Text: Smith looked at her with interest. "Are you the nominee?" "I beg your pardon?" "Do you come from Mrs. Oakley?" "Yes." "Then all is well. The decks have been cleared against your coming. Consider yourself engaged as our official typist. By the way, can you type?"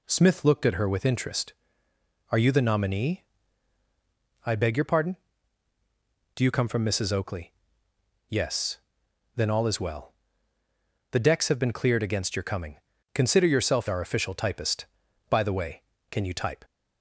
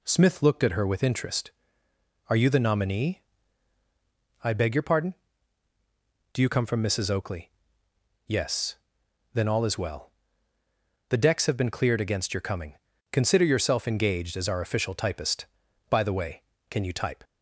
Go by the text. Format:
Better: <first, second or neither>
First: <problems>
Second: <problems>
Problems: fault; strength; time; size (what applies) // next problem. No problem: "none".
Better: second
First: skips "engaged as"; at 13.8 s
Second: none